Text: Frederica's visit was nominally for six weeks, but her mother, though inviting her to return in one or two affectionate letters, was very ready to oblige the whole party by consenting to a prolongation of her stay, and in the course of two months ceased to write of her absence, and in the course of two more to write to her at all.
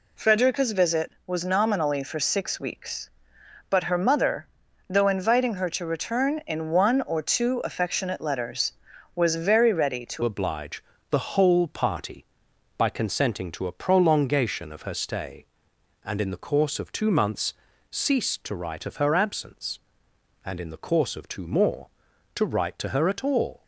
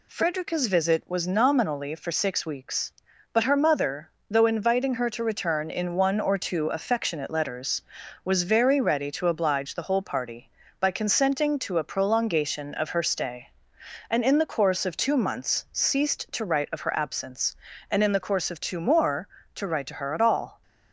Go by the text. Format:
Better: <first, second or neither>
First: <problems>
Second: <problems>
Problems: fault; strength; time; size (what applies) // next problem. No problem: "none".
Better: second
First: changes voice at "oblige"; from 10.2 s on; 13.4 s long // pauses between "oblige" and "the"; slight; at 10.8 s; 0.30 s long // pauses between "months" and "ceased"; at 17.5 s; 0.38 s long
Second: none